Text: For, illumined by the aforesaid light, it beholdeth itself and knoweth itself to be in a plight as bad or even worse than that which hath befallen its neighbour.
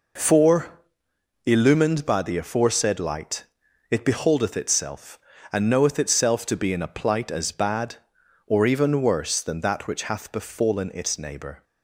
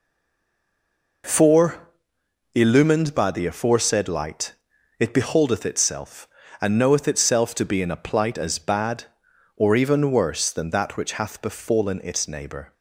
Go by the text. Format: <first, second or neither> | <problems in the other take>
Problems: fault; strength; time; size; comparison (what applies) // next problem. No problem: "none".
first | stays silent before the first word; noticeable; until 1.2 s; 1.2 s long